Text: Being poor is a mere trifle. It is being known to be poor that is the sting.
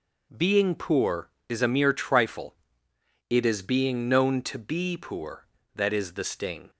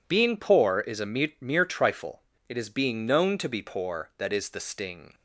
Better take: first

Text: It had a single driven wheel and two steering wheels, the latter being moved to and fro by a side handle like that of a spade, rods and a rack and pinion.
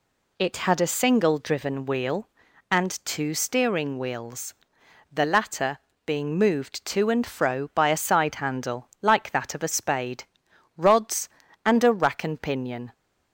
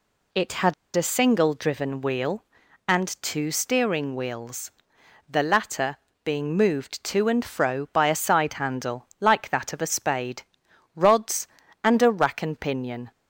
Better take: first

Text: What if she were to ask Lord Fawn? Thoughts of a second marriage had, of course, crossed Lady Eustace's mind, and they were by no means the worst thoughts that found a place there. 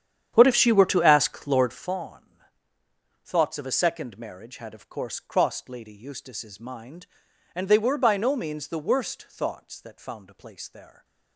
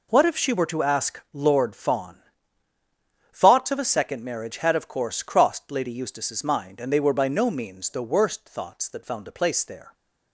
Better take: second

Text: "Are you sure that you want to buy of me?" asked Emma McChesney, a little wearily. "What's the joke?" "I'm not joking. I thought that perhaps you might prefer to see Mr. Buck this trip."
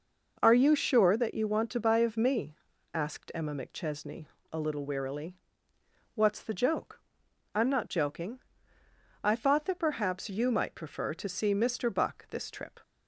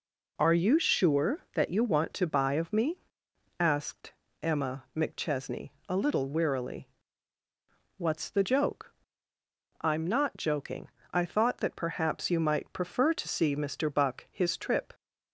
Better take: first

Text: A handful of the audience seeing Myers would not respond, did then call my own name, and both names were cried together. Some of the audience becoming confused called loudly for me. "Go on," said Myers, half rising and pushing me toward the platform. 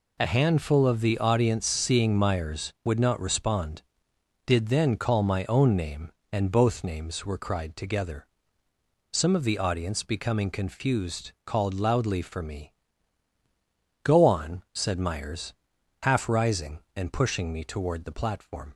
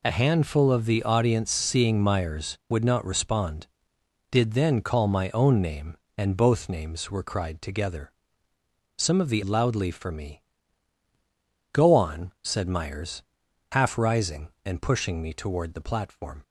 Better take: first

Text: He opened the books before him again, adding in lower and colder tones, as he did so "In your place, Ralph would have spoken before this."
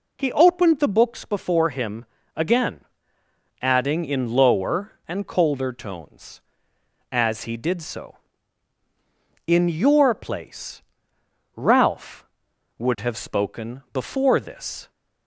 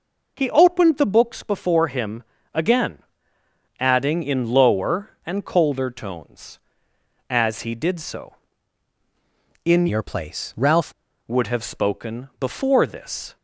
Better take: first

